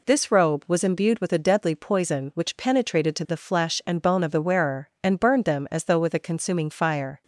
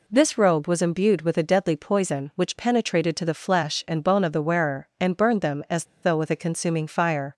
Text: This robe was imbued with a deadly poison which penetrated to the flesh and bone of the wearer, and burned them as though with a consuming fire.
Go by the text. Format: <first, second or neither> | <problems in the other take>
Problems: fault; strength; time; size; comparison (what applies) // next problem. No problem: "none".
first | pauses between "as" and "though"; slight; at 5.8 s; 0.19 s long